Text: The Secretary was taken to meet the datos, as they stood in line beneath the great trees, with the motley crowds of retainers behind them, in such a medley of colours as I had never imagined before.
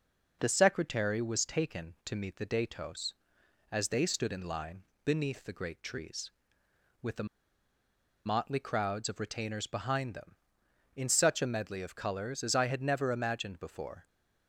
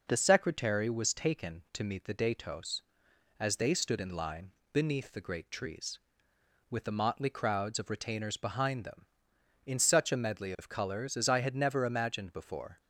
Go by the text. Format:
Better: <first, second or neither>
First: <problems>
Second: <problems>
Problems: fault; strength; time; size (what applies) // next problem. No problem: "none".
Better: second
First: pauses between "line" and "beneath"; slight; at 4.8 s; 0.20 s long // pauses between "the" and "motley"; at 7.2 s; 1.0 s long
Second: pauses between "line" and "beneath"; slight; at 4.5 s; 0.20 s long